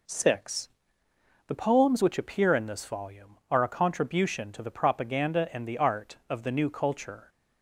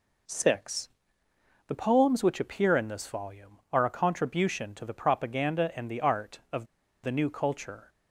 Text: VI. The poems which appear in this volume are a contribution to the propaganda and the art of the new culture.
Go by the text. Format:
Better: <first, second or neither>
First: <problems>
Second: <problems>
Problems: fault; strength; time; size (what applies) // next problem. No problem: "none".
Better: first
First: none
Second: pauses between "of" and "the"; at 6.6 s; 0.37 s long